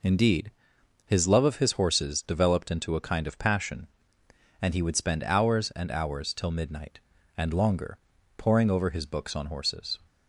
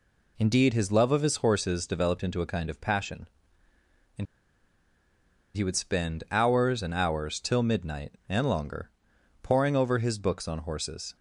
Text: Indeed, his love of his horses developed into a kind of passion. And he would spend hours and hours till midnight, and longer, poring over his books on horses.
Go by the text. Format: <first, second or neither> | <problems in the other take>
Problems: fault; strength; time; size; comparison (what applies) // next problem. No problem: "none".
first | pauses between "And" and "he"; strong; at 4.2 s; 1.2 s long